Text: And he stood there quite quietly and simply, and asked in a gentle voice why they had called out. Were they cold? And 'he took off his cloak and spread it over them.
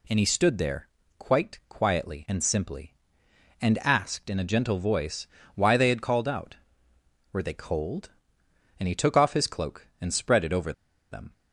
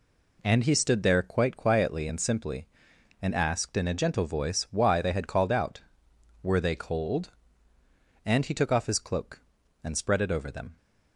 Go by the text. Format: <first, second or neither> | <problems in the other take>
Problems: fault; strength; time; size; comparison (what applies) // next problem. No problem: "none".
second | pauses between "there" and "quite"; slight; at 0.8 s; 0.30 s long // pauses between "voice" and "why"; slight; at 5.2 s; 0.30 s long // pauses between "over" and "them"; at 10.7 s; 0.39 s long